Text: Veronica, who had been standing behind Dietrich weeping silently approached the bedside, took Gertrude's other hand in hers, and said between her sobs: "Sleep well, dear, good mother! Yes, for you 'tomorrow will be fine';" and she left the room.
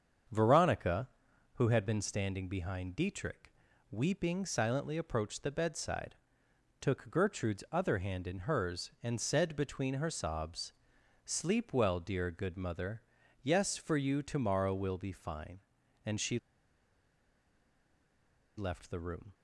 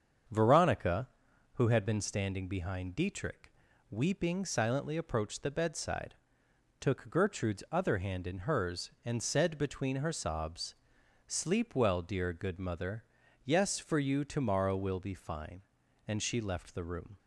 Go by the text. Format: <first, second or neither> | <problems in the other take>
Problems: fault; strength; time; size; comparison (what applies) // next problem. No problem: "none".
second | starts louder than the rest; strong; until 1.7 s; 7 dB; strong in the second // pauses between "Dietrich" and "weeping"; at 3.5 s; 0.38 s long; also in the second // pauses between "she" and "left"; strong; at 16.3 s; 2.1 s long